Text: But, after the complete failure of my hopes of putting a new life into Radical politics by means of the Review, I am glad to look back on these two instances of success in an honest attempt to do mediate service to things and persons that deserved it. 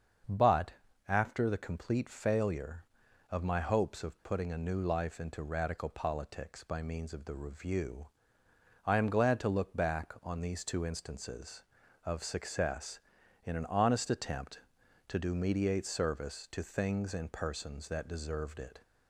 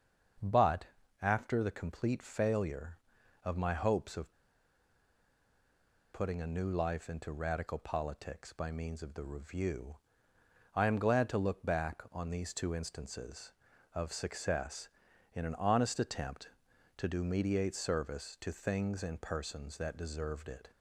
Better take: first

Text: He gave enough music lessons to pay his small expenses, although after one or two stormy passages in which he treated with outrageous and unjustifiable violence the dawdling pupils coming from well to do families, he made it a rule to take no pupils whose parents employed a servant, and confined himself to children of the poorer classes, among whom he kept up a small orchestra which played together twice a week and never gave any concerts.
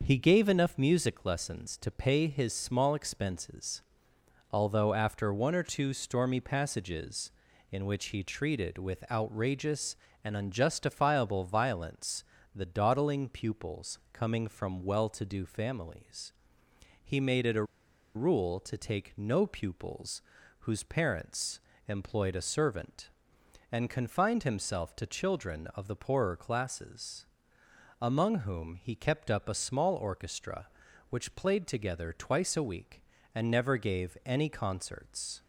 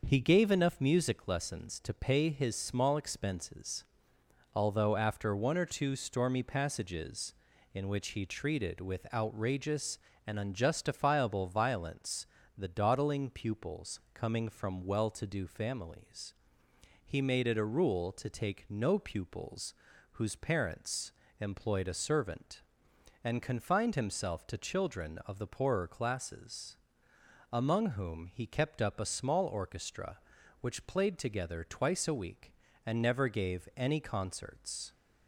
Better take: second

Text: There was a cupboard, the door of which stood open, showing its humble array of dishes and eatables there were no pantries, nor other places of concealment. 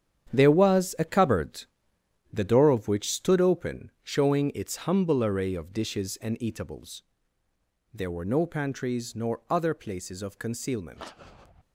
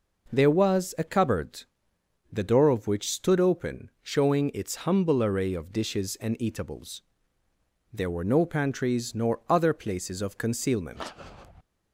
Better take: second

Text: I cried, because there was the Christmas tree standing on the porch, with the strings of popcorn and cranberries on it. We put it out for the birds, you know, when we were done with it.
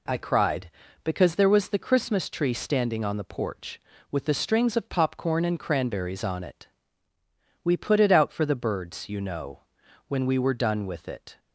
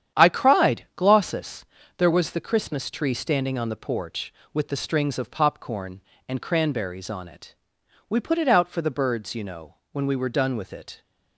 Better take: first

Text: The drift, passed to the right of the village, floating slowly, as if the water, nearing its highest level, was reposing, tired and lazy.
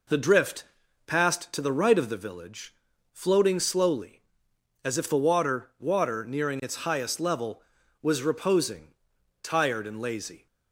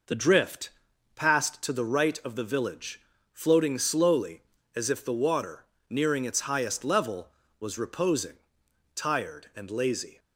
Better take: second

